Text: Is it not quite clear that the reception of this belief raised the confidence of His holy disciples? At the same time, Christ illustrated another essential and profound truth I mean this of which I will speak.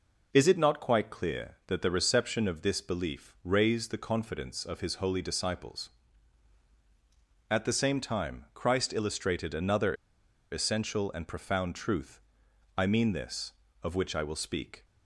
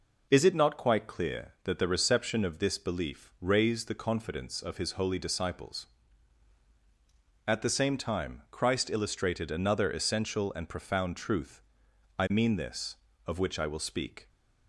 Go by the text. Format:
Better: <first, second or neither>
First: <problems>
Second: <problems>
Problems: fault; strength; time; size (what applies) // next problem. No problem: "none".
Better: second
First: pauses between "another" and "essential"; noticeable; at 9.9 s; 0.58 s long // pauses between "truth" and "I"; noticeable; at 12.2 s; 0.56 s long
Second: pauses between "truth" and "I"; noticeable; at 11.6 s; 0.56 s long